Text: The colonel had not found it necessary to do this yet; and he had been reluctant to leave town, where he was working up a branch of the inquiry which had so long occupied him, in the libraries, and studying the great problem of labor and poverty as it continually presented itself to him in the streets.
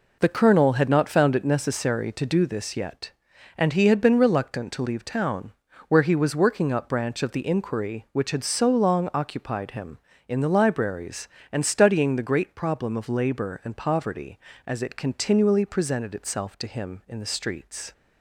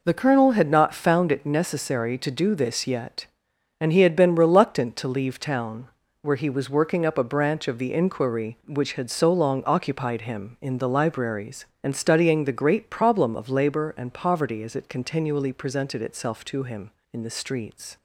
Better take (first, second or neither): second